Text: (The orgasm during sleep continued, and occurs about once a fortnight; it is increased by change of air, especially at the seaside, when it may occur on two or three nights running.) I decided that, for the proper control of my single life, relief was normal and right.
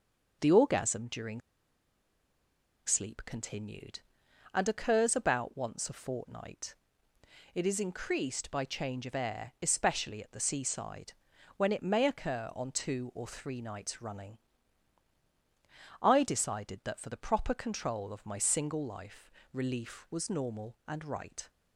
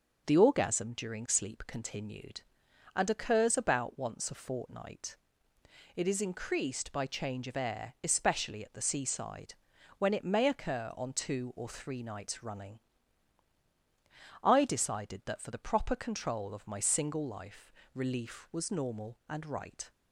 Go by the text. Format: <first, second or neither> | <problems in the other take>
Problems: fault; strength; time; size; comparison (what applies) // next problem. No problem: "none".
second | pauses between "during" and "sleep"; strong; at 1.4 s; 1.4 s long